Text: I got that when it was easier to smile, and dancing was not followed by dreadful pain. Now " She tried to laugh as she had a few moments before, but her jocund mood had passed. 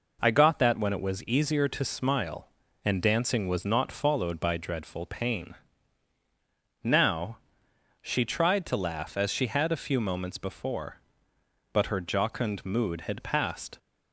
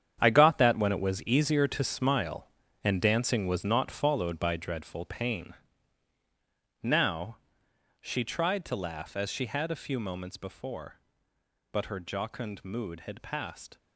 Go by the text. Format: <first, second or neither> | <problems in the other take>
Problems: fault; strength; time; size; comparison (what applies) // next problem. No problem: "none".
first | gets quieter; strong; throughout; 12.5 dB